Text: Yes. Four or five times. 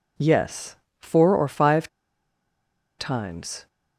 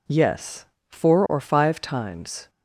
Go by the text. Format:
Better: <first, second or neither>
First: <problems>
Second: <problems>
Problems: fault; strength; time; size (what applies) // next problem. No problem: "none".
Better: second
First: pauses between "five" and "times"; at 1.8 s; 1.1 s long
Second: none